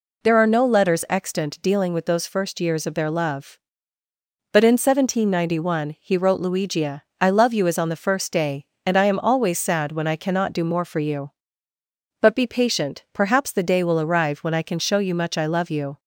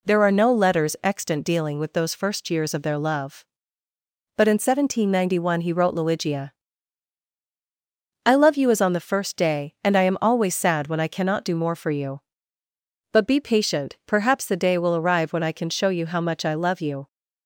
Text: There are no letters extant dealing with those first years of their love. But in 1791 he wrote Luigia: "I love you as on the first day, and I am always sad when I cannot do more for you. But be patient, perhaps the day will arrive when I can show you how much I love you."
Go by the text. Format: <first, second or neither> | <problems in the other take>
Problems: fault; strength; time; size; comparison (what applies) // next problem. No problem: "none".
second | skips "how"; at 15.1 s